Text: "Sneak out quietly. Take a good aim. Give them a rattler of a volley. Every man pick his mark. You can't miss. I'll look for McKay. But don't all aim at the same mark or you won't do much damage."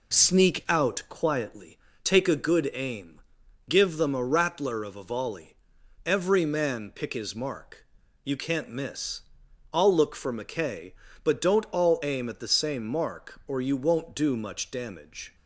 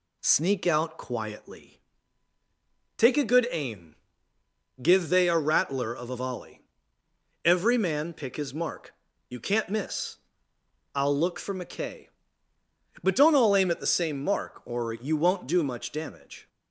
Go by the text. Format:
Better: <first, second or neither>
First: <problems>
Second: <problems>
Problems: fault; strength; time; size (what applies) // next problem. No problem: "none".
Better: first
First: none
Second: says "they" for "them"; at 5.0 s